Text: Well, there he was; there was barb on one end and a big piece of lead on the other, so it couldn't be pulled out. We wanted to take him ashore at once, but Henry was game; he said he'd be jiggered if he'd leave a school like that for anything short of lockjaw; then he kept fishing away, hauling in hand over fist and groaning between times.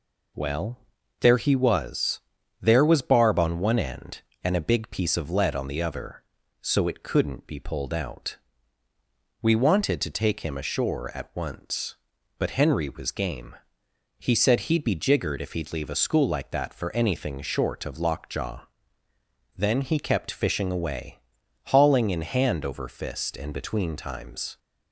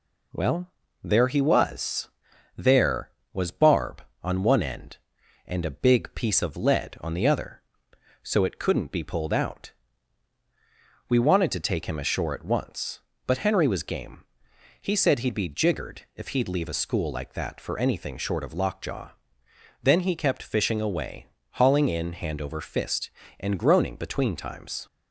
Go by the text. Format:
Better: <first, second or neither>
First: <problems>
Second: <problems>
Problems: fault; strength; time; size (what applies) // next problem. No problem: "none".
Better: second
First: skips "groaning"; at 23.5 s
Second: none